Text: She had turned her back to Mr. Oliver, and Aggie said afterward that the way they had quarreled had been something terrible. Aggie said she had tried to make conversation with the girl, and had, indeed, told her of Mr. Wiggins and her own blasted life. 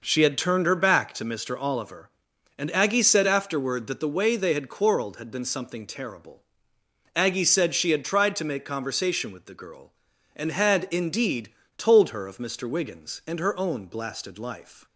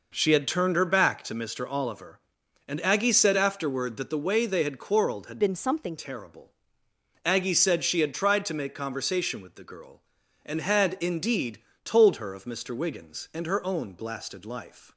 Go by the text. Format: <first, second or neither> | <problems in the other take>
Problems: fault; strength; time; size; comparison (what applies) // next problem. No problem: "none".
first | changes voice from "been" to "something"; from 5.3 to 5.9 s; 0.6 s long